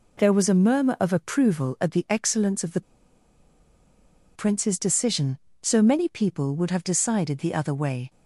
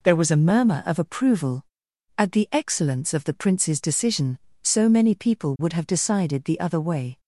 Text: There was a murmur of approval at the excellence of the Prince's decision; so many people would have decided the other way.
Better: second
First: pauses between "the" and "Prince's"; strong; at 2.8 s; 1.5 s long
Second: none

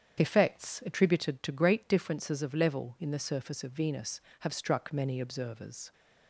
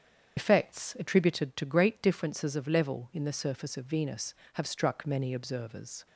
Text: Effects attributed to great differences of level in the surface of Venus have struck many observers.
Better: first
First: starts louder than the rest; strong; until 1.2 s; 8 dB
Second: loses the start of "Effects"; at 0.3 s; 60 ms // starts louder than the rest; strong; until 1.3 s; 8 dB

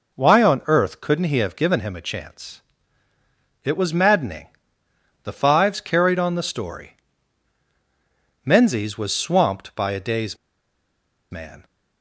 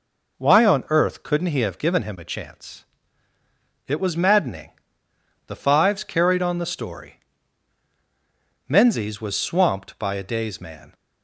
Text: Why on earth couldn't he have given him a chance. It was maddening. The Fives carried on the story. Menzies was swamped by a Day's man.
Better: second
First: pauses between "Day's" and "man"; noticeable; at 10.3 s; 0.94 s long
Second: none

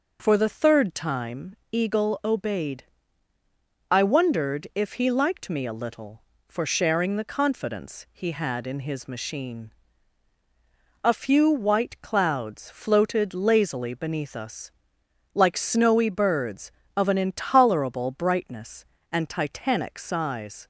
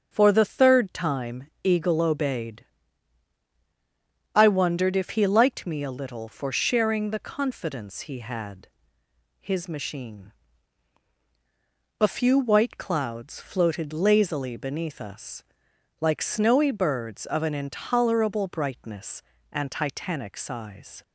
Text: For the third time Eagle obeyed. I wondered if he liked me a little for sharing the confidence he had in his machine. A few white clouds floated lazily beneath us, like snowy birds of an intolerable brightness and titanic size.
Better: first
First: pauses between "time" and "Eagle"; slight; at 1.5 s; 0.16 s long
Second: starts louder than the rest; until 1.1 s; 7 dB // pauses between "time" and "Eagle"; slight; at 1.4 s; 0.20 s long // skips "in"; at 9.0 s

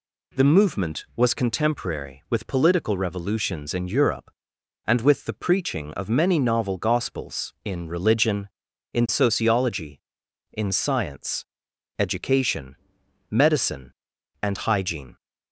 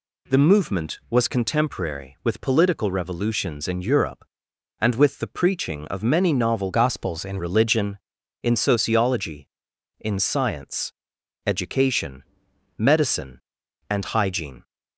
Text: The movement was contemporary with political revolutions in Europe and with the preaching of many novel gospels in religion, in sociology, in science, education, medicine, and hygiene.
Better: first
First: none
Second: changes voice from "gospels" to "in"; from 6.7 to 7.3 s; 0.6 s long

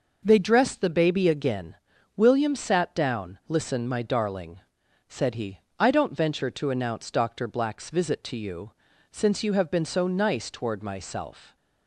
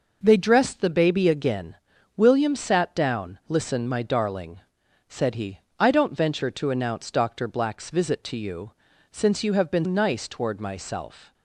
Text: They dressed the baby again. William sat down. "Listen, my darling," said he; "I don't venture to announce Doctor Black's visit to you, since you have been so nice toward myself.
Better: first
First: none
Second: skips "so"; at 9.8 s

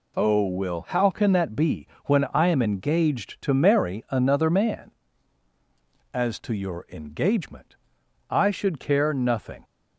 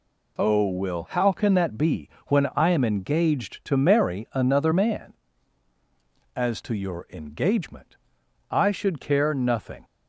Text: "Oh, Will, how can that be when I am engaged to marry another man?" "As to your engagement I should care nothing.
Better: neither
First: pauses between "be" and "when"; slight; at 1.8 s; 0.16 s long // pauses between "engagement" and "I"; noticeable; at 7.7 s; 0.56 s long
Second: pauses between "be" and "when"; slight; at 2.1 s; 0.16 s long // pauses between "engagement" and "I"; noticeable; at 7.9 s; 0.56 s long

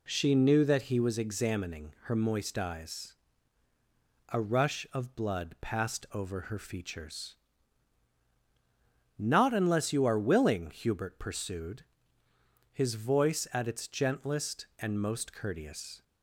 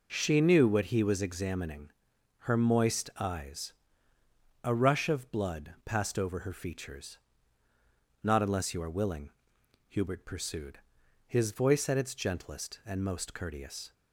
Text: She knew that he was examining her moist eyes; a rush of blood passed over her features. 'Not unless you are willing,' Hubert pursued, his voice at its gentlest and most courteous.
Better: first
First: none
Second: says "what" for "that"; at 0.6 s // pauses between "examining" and "her"; noticeable; at 1.8 s; 0.50 s long

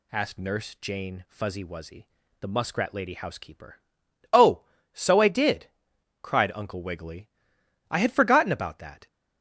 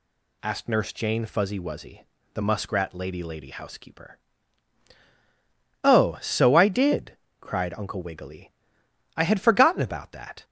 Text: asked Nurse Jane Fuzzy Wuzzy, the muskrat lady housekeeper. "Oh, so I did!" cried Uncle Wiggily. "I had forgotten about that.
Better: first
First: none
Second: says "lady" twice; at 3.2 s

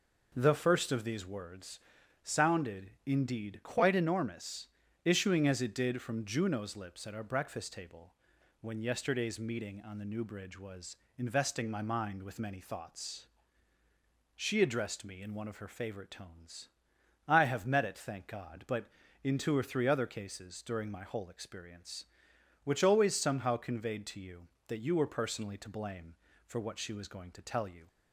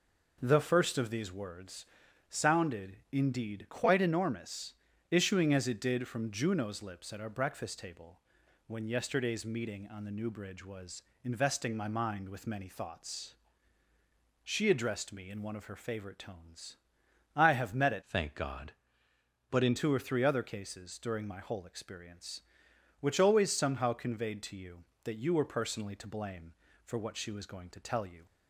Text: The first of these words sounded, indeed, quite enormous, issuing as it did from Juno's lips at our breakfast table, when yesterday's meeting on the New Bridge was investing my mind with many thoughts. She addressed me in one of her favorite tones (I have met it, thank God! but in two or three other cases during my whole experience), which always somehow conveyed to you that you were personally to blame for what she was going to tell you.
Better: first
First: pauses between "words" and "sounded"; at 1.7 s; 0.44 s long // pauses between "was" and "investing"; slight; at 10.9 s; 0.24 s long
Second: pauses between "words" and "sounded"; at 1.8 s; 0.44 s long // pauses between "was" and "investing"; slight; at 11.0 s; 0.24 s long // changes voice from "thank" to "in"; from 18.0 to 19.7 s; 1.7 s long

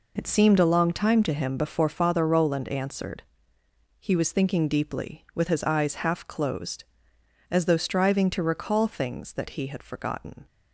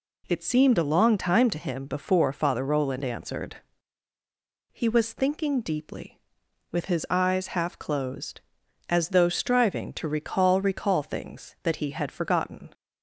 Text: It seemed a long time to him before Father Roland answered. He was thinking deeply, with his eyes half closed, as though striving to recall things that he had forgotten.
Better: first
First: none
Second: says "recall" twice; at 10.6 s

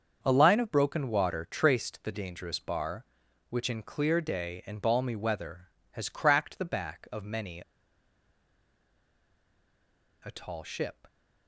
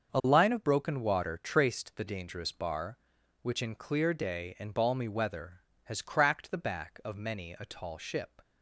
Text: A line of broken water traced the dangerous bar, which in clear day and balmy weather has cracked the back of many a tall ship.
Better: second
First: starts louder than the rest; until 1.2 s; 6.5 dB // pauses between "many" and "a"; strong; at 7.6 s; 2.6 s long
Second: starts louder than the rest; until 1.1 s; 6.5 dB

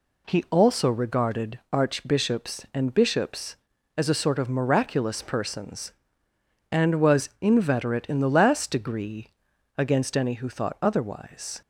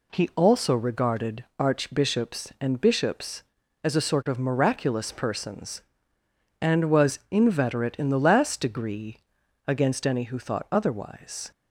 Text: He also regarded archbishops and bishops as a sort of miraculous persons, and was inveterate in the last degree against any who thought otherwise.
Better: neither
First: pauses between "degree" and "against"; noticeable; at 9.2 s; 0.50 s long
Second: pauses between "degree" and "against"; noticeable; at 9.1 s; 0.50 s long

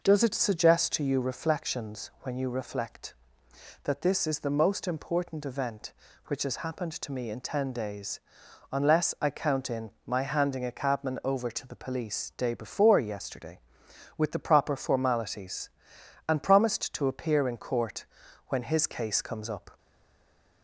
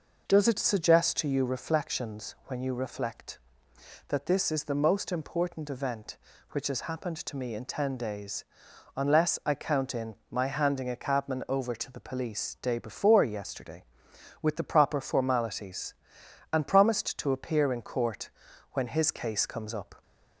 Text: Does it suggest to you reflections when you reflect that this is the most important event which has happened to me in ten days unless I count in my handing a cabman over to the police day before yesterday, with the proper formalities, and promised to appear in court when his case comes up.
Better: second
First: pauses between "days" and "unless"; noticeable; at 8.1 s; 0.52 s long // pauses between "in" and "my"; slight; at 9.9 s; 0.16 s long // pauses between "court" and "when"; at 18.0 s; 0.40 s long // stays silent after the last word; slight; from 19.7 s on; 0.9 s long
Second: pauses between "days" and "unless"; noticeable; at 8.4 s; 0.52 s long // pauses between "in" and "my"; slight; at 10.1 s; 0.16 s long // pauses between "court" and "when"; at 18.3 s; 0.40 s long

